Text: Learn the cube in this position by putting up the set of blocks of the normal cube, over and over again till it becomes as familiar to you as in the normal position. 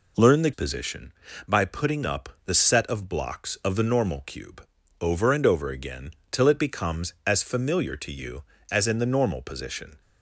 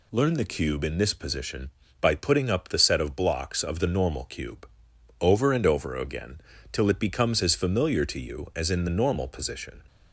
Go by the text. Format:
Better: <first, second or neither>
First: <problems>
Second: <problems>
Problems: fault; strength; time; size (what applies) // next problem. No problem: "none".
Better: second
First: skips "cube in this"; at 0.5 s // pauses between "up" and "the"; slight; at 2.2 s; 0.18 s long // pauses between "again" and "till"; slight; at 6.0 s; 0.22 s long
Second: pauses between "again" and "till"; slight; at 6.3 s; 0.32 s long